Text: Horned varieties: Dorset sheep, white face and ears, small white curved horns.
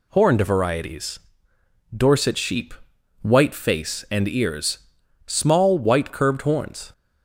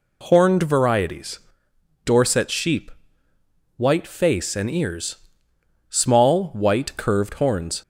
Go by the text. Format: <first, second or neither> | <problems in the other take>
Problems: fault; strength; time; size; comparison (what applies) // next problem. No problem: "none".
neither | none